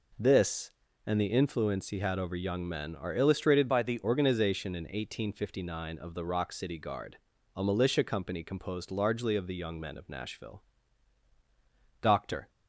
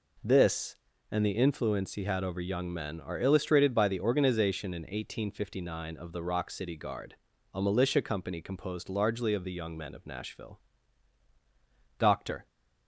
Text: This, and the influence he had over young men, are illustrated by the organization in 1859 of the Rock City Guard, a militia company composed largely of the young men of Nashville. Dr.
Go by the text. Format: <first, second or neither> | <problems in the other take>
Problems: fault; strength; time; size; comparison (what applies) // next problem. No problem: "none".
second | changes voice from "by" to "the"; from 3.6 to 3.9 s; 0.3 s long